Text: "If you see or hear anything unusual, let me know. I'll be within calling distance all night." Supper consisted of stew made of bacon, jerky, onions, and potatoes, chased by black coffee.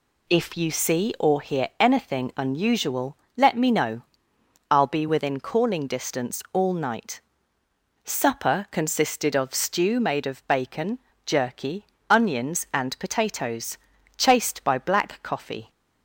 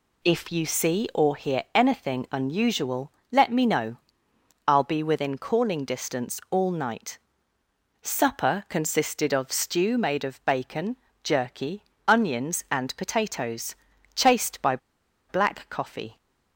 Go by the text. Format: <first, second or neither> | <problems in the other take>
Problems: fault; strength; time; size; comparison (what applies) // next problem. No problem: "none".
first | pauses between "by" and "black"; noticeable; at 14.7 s; 0.51 s long